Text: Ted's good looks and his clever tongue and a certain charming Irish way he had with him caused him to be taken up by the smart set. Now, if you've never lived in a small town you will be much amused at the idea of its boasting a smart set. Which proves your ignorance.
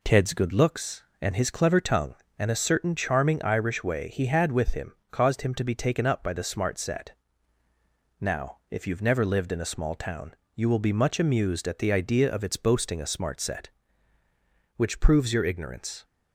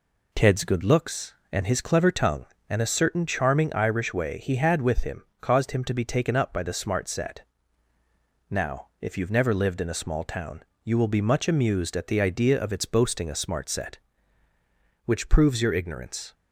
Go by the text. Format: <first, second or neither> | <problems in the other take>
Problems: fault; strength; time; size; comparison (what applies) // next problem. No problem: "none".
neither | pauses between "him" and "caused"; slight; the same in both // pauses between "town" and "you"; slight; the same in both